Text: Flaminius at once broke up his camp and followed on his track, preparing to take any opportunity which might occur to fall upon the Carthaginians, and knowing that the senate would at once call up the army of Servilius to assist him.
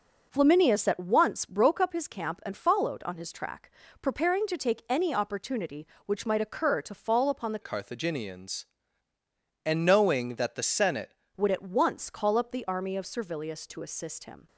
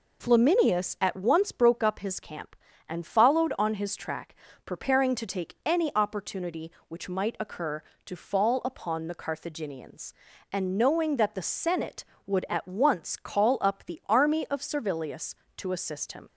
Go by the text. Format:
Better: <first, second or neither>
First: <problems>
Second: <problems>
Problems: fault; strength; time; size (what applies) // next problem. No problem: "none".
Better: second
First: changes voice from "Carthaginians" to "senate"; from 7.6 to 11.1 s; 3.5 s long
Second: none